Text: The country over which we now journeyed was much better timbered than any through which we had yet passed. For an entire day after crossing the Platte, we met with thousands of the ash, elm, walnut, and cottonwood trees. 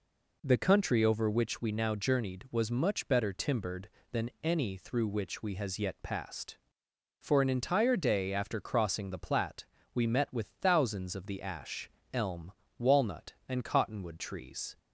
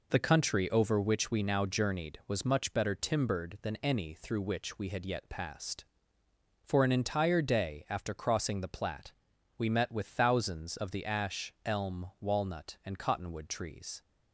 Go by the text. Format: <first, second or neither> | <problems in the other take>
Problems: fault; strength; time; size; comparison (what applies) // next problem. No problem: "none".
second | says "has" for "had"; at 5.5 s